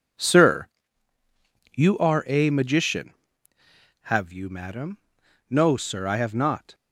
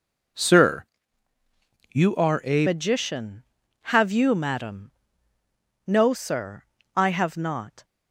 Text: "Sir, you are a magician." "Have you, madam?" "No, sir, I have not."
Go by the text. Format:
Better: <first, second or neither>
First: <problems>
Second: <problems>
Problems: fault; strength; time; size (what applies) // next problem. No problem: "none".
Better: first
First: none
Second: changes voice at "magician"; from 2.6 s on; 5.2 s long